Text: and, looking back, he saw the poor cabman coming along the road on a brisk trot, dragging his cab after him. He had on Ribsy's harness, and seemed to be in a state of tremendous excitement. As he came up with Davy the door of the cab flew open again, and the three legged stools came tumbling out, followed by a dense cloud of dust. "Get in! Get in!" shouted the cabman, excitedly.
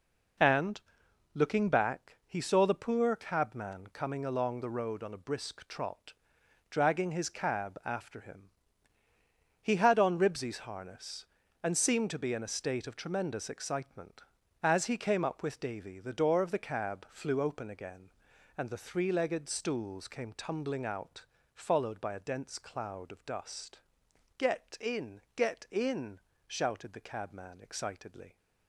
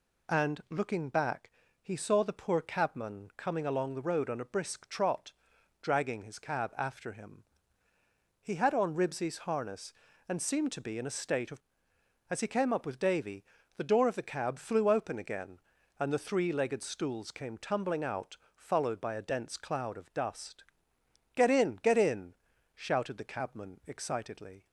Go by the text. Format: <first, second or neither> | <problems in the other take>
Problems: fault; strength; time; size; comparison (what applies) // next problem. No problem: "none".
first | skips "tremendous excitement"; at 11.9 s // pauses between "Davy" and "the"; slight; at 13.4 s; 0.32 s long